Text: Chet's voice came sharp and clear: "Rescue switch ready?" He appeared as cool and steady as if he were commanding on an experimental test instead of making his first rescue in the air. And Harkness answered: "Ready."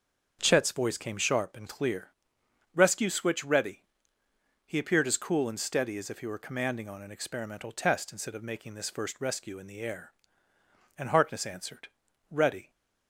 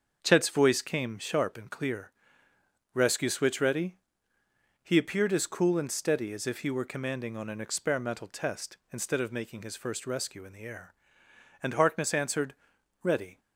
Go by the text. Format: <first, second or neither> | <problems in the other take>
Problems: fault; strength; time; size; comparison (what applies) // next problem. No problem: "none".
second | starts louder than the rest; until 1.4 s; 6.5 dB; also in the second // says "this" for "his"; at 8.7 s